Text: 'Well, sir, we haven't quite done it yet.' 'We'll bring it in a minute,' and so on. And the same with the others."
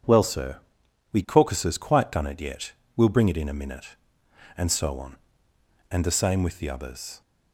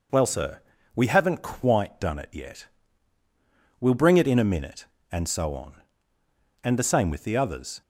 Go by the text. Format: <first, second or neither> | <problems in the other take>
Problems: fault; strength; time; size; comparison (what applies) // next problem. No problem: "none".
second | says "caucuses" for "haven't"; at 1.2 s